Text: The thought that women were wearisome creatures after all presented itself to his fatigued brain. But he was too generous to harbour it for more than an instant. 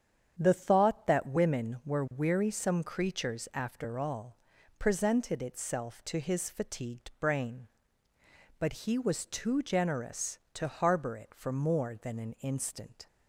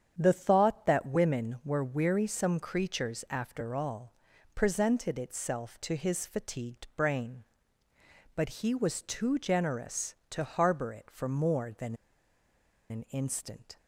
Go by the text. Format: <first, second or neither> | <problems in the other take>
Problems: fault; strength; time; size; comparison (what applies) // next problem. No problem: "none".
first | starts louder than the rest; strong; until 1.1 s; 8 dB; strong in the first // pauses between "all" and "presented"; at 4.1 s; 0.40 s long; also in the first // pauses between "than" and "an"; noticeable; at 11.9 s; 0.95 s long